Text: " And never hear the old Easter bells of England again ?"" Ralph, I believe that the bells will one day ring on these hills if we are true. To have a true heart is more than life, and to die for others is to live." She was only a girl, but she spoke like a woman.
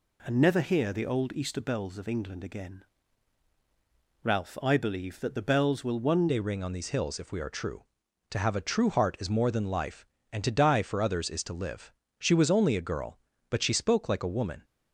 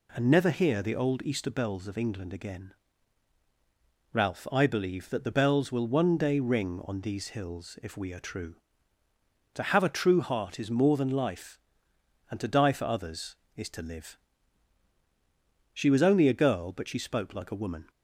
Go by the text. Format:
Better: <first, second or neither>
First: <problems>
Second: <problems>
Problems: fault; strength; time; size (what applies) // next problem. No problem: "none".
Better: second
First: changes voice at "day"; from 6.2 s on; 8.4 s long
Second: none